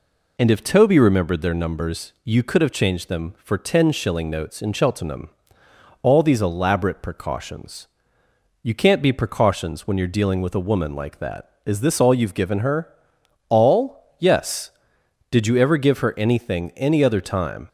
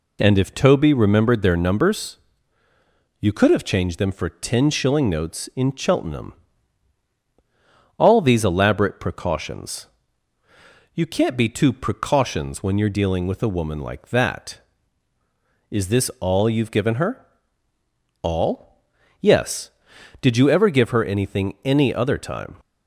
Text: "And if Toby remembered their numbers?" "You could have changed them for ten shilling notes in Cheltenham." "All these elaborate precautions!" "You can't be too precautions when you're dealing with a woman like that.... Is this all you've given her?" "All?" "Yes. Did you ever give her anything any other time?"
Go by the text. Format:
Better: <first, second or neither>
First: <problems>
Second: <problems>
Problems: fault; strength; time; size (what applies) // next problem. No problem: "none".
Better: second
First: skips "too"; at 9.1 s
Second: none